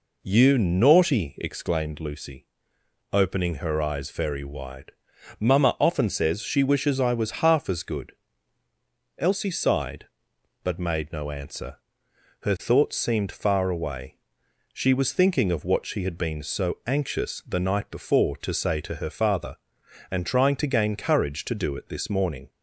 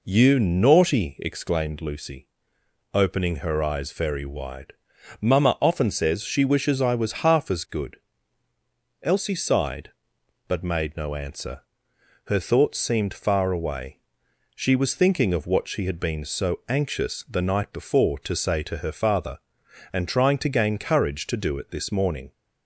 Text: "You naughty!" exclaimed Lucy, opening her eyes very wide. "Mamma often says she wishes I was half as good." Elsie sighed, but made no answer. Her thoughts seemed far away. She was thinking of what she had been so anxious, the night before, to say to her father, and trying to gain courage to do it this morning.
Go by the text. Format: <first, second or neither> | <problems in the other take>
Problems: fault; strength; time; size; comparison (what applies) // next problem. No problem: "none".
neither | none